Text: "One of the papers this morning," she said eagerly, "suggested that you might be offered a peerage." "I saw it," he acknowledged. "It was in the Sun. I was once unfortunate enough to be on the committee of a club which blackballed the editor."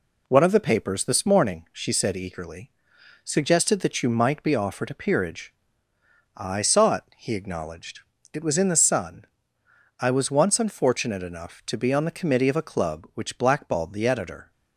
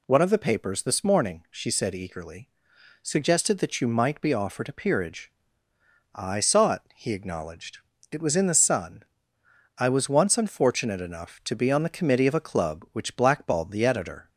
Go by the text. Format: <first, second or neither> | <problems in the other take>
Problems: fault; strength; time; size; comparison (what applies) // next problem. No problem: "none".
second | gets quieter; slight; throughout; 3 dB